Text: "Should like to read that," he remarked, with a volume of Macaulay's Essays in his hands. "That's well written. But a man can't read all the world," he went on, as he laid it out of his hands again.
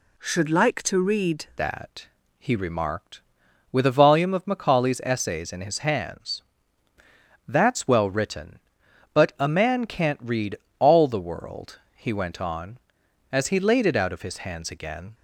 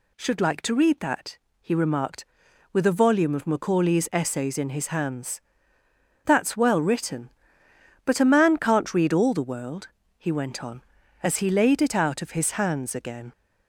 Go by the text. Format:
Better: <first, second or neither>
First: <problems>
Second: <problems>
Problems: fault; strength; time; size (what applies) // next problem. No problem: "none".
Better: second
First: changes voice at "that"; from 1.5 s on; 13.6 s long // pauses between "read" and "all"; slight; at 10.5 s; 0.22 s long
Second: none